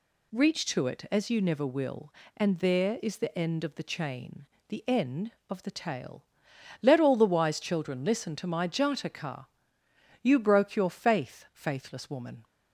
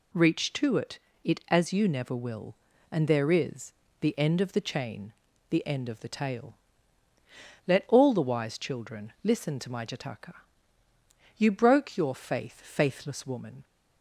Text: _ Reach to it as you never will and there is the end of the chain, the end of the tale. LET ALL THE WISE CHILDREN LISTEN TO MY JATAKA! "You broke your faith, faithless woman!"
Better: first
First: none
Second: says "it" twice; at 1.2 s // pauses between "is" and "the"; slight; at 3.7 s; 0.30 s long

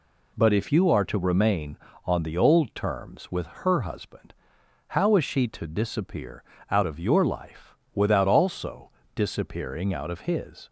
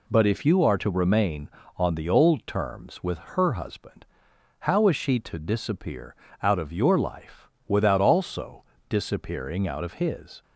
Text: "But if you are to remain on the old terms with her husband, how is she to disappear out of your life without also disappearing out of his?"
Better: neither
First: pauses between "disappear" and "out"; slight; at 6.4 s; 0.28 s long // pauses between "life" and "without"; slight; at 7.7 s; 0.18 s long // pauses between "also" and "disappearing"; slight; at 8.8 s; 0.23 s long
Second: pauses between "disappear" and "out"; slight; at 6.1 s; 0.28 s long // pauses between "life" and "without"; slight; at 7.4 s; 0.18 s long // pauses between "also" and "disappearing"; slight; at 8.6 s; 0.24 s long

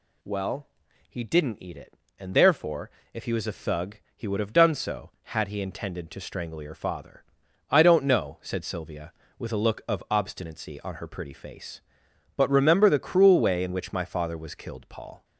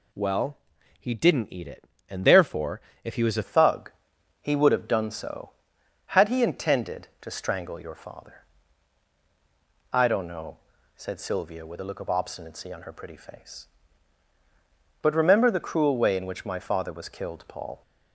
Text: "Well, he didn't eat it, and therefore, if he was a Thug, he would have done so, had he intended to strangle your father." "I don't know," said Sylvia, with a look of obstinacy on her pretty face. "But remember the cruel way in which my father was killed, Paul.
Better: first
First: none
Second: changes voice at "Thug"; from 3.4 s on; 14.4 s long

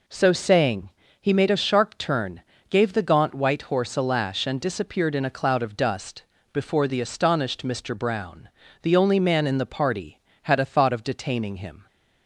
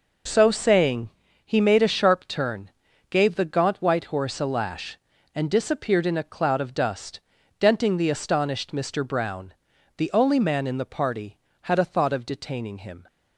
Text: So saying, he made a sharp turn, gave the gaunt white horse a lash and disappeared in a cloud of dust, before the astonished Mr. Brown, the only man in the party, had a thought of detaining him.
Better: first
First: none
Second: says "denting" for "before"; at 7.6 s

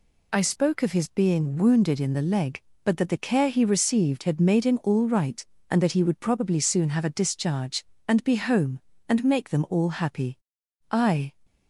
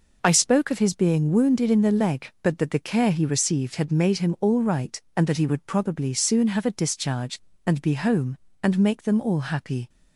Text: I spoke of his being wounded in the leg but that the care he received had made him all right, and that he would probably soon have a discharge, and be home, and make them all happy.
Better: second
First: goes on to say "I"; slight; from 10.9 s on; 0.42 s long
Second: none

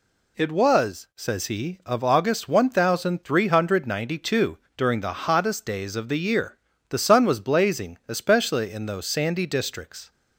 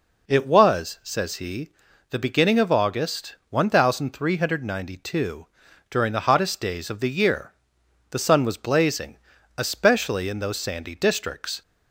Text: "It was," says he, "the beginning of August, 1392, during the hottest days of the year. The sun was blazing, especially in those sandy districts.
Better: second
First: skips "the beginning"; at 1.8 s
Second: none

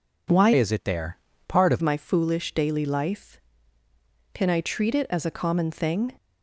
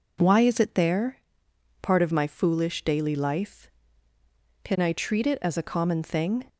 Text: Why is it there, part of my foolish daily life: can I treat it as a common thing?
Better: second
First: changes voice from "is" to "of"; from 0.5 to 1.7 s; 1.2 s long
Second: none

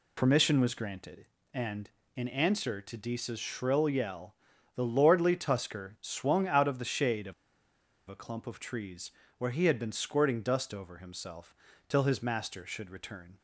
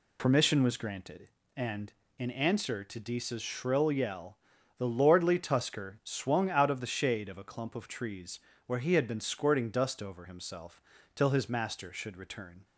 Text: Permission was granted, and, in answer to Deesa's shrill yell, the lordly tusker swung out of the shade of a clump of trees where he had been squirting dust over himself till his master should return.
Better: second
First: pauses between "of" and "a"; noticeable; at 7.3 s; 0.75 s long // pauses between "trees" and "where"; slight; at 9.0 s; 0.28 s long // pauses between "himself" and "till"; slight; at 11.5 s; 0.34 s long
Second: pauses between "trees" and "where"; slight; at 8.3 s; 0.28 s long // pauses between "himself" and "till"; slight; at 10.8 s; 0.34 s long

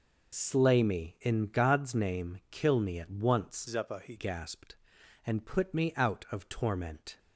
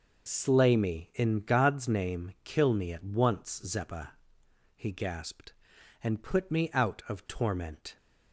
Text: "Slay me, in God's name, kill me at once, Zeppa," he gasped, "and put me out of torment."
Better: second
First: changes voice from "Zeppa" to "he"; from 3.6 to 4.1 s; 0.5 s long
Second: none

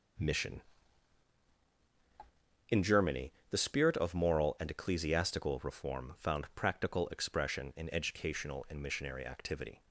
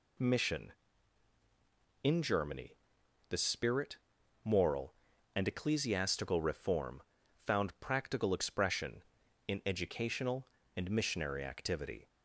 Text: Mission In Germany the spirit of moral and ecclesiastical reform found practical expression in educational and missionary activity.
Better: first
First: pauses between "Germany" and "the"; slight; at 3.3 s; 0.18 s long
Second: pauses between "Germany" and "the"; noticeable; at 2.7 s; 0.56 s long // skips "of"; at 4.2 s // pauses between "reform" and "found"; at 7.0 s; 0.44 s long

